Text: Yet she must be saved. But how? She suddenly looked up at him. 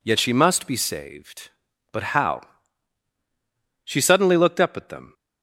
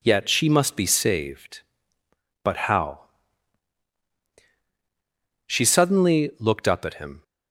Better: second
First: says "them" for "him"; at 4.8 s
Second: none

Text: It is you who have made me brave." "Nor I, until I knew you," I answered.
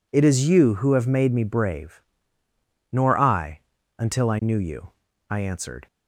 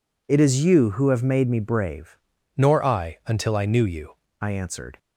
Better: first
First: none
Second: changes voice from "Nor" to "you"; from 2.5 to 4.1 s; 1.6 s long

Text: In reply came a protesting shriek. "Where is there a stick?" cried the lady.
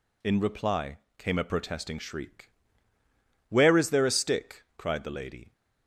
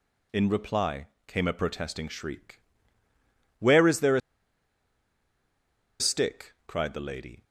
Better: first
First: pauses between "reply" and "came"; slight; at 0.9 s; 0.18 s long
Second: pauses between "reply" and "came"; slight; at 1.0 s; 0.18 s long // pauses between "a" and "stick"; strong; at 4.2 s; 1.8 s long

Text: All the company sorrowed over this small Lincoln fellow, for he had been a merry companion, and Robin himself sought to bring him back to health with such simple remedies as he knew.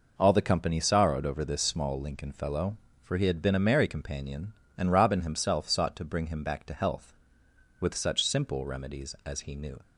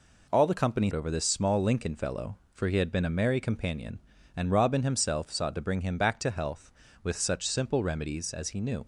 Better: first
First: none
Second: skips "sorrowed"; at 0.9 s

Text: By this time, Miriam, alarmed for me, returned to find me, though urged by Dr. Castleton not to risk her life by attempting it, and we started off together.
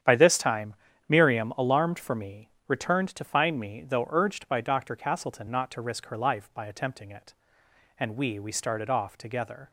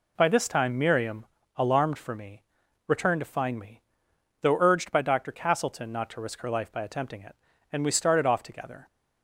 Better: second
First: starts louder than the rest; strong; until 1.3 s; 9 dB // says "we" twice; at 8.3 s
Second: none

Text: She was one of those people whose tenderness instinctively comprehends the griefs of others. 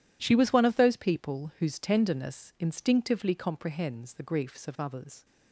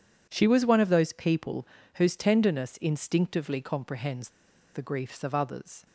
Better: first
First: none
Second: pauses between "people" and "whose"; slight; at 1.6 s; 0.30 s long // pauses between "comprehends" and "the"; at 4.2 s; 0.44 s long

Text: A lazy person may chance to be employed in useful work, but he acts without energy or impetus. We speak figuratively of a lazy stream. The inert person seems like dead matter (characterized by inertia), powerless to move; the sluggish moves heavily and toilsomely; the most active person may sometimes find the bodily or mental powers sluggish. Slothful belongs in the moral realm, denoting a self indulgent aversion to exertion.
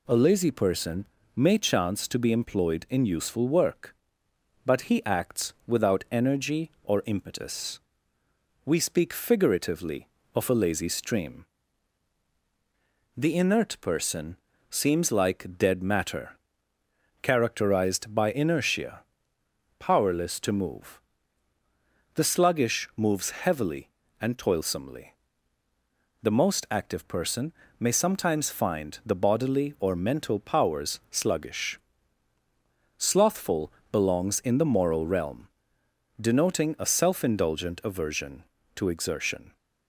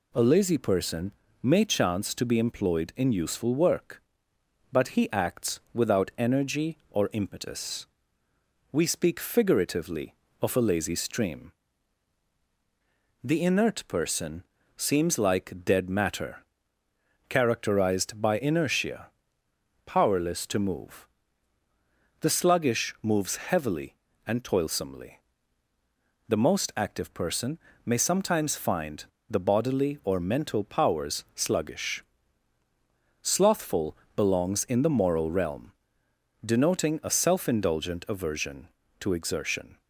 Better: first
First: pauses between "person" and "may"; slight; at 1.0 s; 0.30 s long // pauses between "person" and "seems"; slight; at 14.3 s; 0.32 s long // pauses between "person" and "may"; slight; at 27.5 s; 0.28 s long // pauses between "Slothful" and "belongs"; slight; at 33.7 s; 0.20 s long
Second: pauses between "person" and "may"; slight; at 1.1 s; 0.30 s long // pauses between "person" and "seems"; slight; at 14.4 s; 0.32 s long // pauses between "person" and "may"; slight; at 27.5 s; 0.28 s long // pauses between "find" and "the"; slight; at 29.0 s; 0.24 s long // pauses between "Slothful" and "belongs"; slight; at 33.9 s; 0.20 s long

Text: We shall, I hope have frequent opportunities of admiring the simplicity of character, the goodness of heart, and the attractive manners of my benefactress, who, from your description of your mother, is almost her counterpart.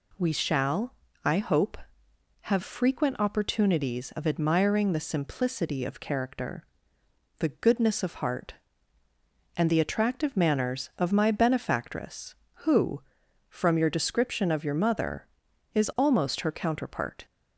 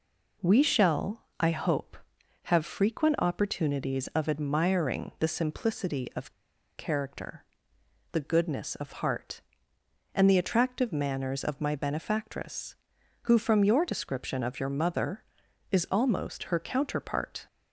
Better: first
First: none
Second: pauses between "of" and "character"; at 6.3 s; 0.44 s long

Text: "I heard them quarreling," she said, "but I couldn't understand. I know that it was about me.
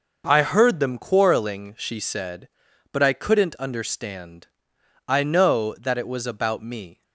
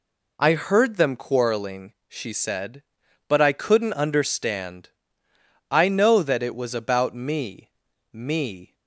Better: first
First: none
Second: says "me" twice; at 8.1 s

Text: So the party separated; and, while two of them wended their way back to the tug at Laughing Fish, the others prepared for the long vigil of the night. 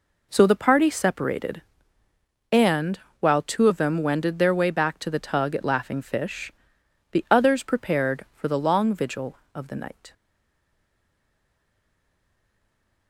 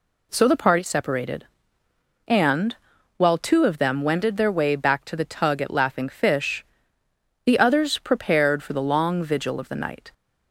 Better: second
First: stays silent after the last word; strong; from 10.1 s on; 2.9 s long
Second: none

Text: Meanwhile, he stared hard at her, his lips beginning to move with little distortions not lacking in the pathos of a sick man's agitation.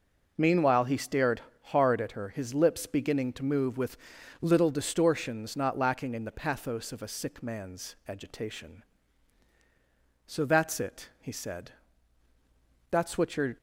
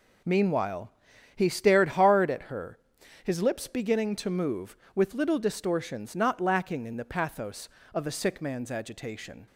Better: second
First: pauses between "stared" and "hard"; slight; at 1.4 s; 0.28 s long // pauses between "with" and "little"; noticeable; at 3.9 s; 0.46 s long // goes on to say "So that's it he said That's what you're"; strong; from 10.2 s on; 3.3 s long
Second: none

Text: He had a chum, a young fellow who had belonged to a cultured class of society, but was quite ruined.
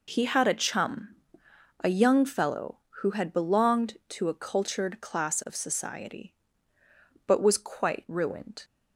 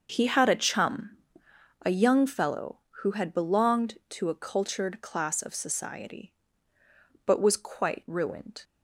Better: first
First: none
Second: starts louder than the rest; noticeable; until 1.2 s; 6 dB

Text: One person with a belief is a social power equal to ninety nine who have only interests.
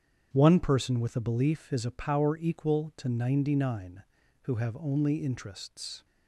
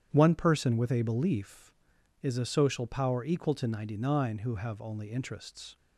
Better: second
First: starts louder than the rest; strong; until 1.3 s; 8 dB // skips "social"; at 1.9 s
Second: starts louder than the rest; strong; until 1.1 s; 9.5 dB

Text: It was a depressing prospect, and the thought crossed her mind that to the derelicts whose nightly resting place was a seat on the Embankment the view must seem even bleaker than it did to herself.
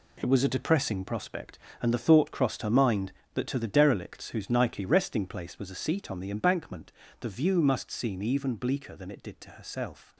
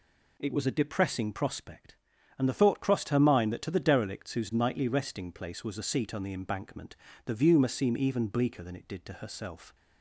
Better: second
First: gets quieter; strong; throughout; 10 dB // pauses between "Embankment" and "the"; slight; at 6.9 s; 0.28 s long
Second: pauses between "Embankment" and "the"; slight; at 6.9 s; 0.28 s long

